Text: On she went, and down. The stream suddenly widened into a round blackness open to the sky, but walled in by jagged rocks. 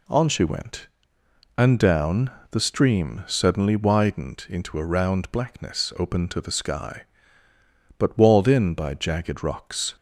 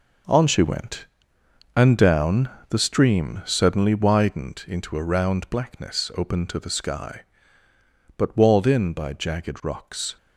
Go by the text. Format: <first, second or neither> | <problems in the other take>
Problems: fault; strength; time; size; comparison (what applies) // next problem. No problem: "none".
first | gets quieter; strong; throughout; 9.5 dB